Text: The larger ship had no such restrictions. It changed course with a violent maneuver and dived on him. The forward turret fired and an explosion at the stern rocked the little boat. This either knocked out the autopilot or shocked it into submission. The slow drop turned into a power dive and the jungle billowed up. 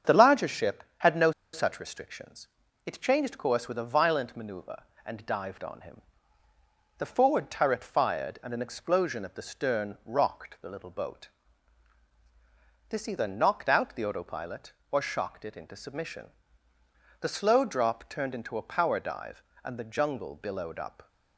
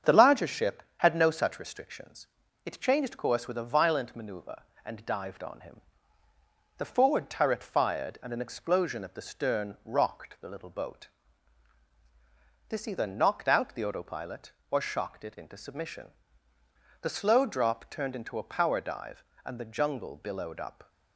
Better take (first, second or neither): second